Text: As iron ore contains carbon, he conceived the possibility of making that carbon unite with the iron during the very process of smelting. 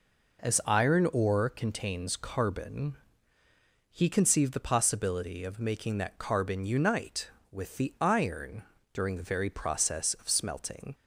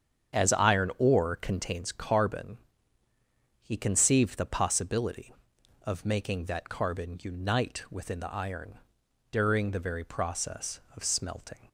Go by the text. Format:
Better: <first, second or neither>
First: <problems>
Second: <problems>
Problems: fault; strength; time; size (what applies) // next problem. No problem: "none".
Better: first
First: pauses between "iron" and "during"; slight; at 8.6 s; 0.32 s long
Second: starts louder than the rest; strong; until 1.4 s; 8 dB // says "within" for "with"; at 7.8 s // pauses between "iron" and "during"; noticeable; at 8.7 s; 0.50 s long